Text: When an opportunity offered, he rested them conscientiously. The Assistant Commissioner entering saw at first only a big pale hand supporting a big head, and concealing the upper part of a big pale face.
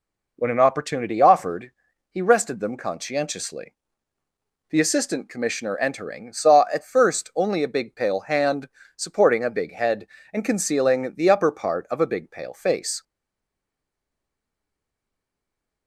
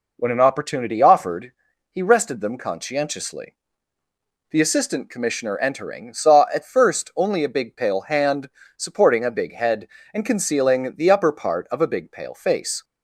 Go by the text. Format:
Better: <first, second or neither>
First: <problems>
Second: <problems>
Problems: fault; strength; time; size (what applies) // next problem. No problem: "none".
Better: second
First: pauses between "hand" and "supporting"; slight; at 8.6 s; 0.30 s long // stays silent after the last word; strong; from 13.0 s on; 2.8 s long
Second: pauses between "hand" and "supporting"; slight; at 8.4 s; 0.30 s long